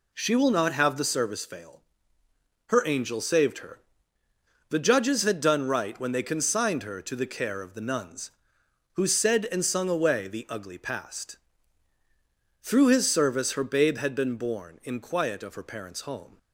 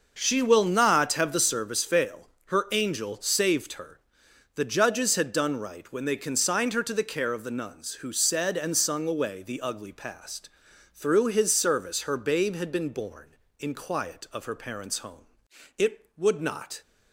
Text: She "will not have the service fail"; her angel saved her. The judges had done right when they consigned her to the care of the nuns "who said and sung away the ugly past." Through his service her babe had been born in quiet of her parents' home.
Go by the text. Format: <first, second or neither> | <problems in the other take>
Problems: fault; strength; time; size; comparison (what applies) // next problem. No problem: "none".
first | goes on to say "It would not"; noticeable; from 15.7 s on; 1.0 s long